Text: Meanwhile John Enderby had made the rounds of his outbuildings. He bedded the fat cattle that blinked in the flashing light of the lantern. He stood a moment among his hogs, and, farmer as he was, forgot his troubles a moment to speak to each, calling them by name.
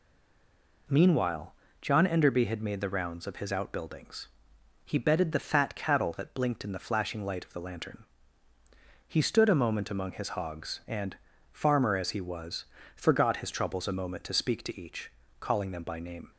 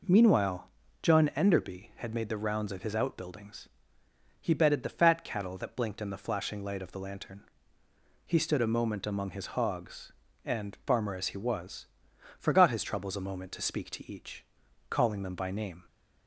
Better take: second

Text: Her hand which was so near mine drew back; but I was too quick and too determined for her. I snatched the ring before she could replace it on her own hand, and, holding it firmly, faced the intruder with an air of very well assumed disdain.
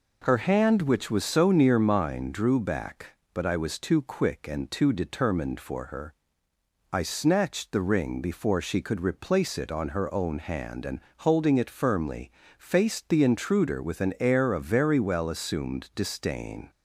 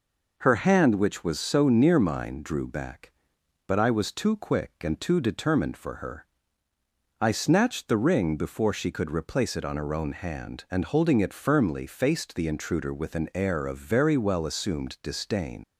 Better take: first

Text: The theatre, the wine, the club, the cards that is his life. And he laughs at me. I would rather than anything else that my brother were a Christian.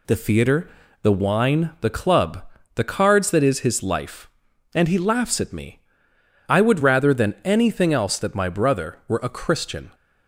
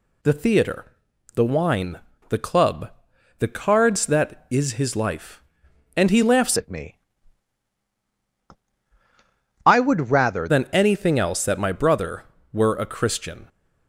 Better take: first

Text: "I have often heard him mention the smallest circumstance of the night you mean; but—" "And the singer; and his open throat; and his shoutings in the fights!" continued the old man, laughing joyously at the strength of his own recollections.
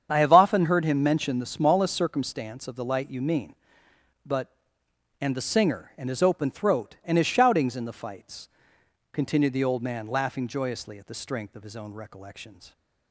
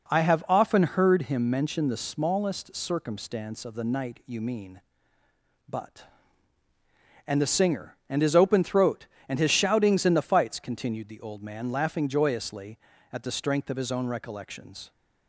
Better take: second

